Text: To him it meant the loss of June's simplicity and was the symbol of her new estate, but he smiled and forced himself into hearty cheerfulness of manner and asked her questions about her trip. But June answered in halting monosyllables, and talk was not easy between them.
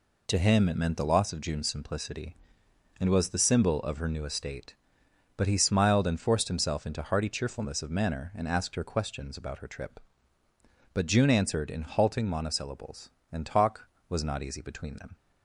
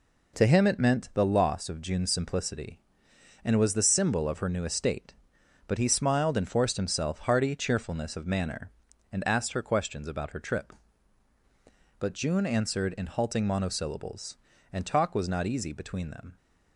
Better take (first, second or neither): first